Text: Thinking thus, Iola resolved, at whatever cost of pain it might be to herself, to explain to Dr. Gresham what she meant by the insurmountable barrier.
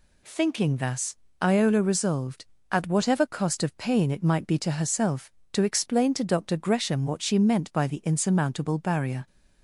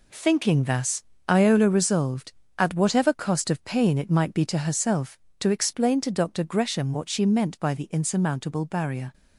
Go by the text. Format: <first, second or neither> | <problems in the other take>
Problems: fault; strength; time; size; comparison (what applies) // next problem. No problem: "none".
first | gets quieter; throughout; 7 dB